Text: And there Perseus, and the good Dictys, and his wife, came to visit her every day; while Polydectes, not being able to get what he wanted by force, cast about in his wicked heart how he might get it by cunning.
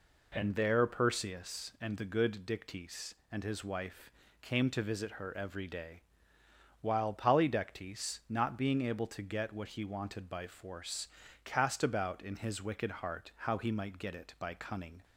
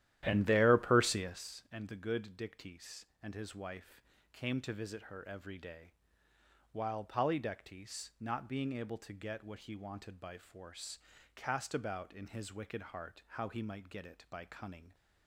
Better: first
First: none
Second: starts louder than the rest; strong; until 1.5 s; 12.5 dB

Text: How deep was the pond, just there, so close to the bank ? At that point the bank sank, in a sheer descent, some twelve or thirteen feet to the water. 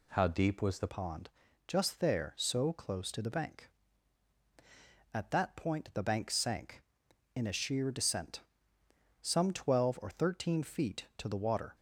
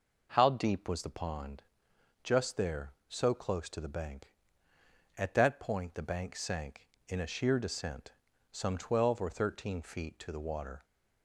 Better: second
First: changes voice at "pond"; from 0.8 s on; 10.9 s long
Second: none

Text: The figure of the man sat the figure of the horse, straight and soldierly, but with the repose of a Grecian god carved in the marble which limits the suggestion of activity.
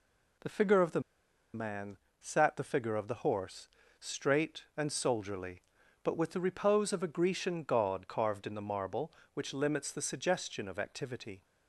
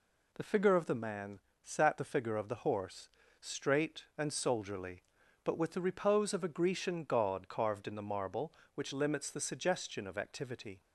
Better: second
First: pauses between "the" and "man"; noticeable; at 0.9 s; 0.54 s long // pauses between "man" and "sat"; slight; at 1.9 s; 0.22 s long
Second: pauses between "man" and "sat"; slight; at 1.3 s; 0.22 s long

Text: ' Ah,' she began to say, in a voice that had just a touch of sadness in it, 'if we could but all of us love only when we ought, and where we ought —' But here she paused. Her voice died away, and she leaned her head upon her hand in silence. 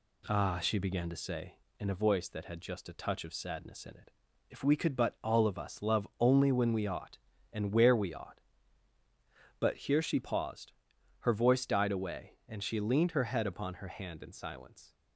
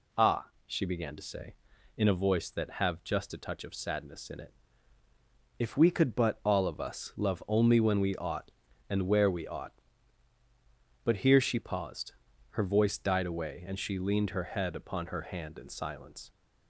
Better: first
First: none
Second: says "have" for "had"; at 2.7 s

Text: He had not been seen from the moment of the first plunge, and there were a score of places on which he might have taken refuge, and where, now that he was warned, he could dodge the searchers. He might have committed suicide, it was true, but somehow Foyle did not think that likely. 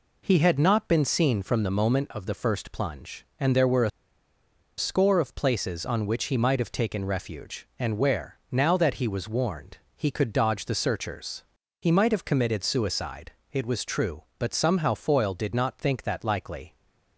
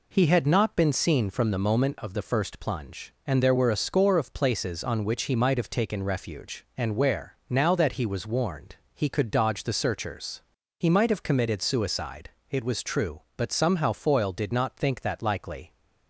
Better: second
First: pauses between "a" and "score"; noticeable; at 3.9 s; 0.87 s long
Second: none

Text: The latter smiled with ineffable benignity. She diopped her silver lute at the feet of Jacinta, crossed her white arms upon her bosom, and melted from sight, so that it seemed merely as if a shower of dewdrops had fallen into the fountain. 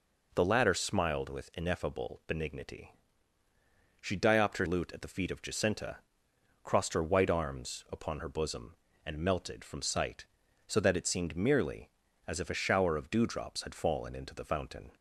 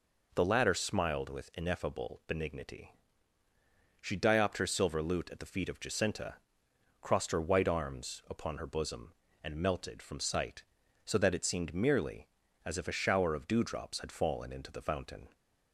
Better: second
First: skips "silver"; at 4.6 s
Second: none

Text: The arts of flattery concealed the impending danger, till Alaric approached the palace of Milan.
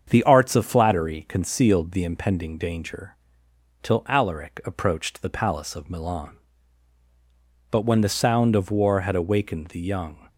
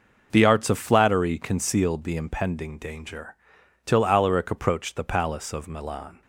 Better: second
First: starts louder than the rest; strong; until 1.1 s; 7.5 dB // goes on to say "But when the sound of war had awakened the young"; strong; from 7.7 s on; 2.5 s long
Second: none

